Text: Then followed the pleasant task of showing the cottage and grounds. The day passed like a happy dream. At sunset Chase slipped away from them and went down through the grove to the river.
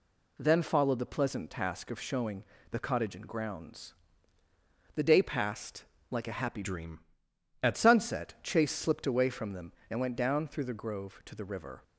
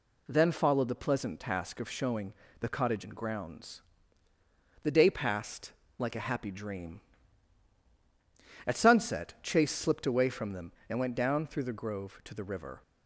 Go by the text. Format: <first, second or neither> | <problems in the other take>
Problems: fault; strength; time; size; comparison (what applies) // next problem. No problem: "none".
second | pauses between "showing" and "the"; slight; at 2.4 s; 0.28 s long; slight in the second // pauses between "passed" and "like"; slight; at 5.8 s; 0.26 s long; slight in the second // changes voice from "dream" to "At"; from 6.6 to 7.7 s; 1.1 s long